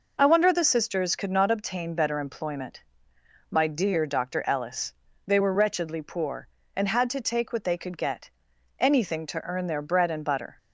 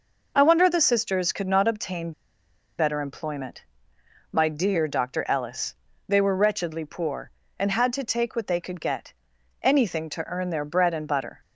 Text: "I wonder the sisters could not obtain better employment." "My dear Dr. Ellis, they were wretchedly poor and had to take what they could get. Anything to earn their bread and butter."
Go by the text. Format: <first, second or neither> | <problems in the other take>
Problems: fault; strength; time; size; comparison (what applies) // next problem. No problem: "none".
first | pauses between "obtain" and "better"; noticeable; at 2.1 s; 0.67 s long